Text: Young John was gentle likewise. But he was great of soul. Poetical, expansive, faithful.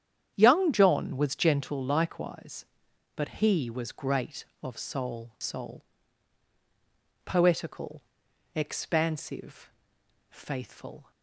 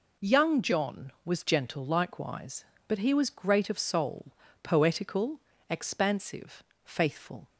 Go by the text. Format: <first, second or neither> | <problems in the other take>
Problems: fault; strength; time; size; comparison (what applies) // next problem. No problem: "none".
second | starts louder than the rest; strong; until 1.3 s; 9 dB // says "soul" twice; at 5.3 s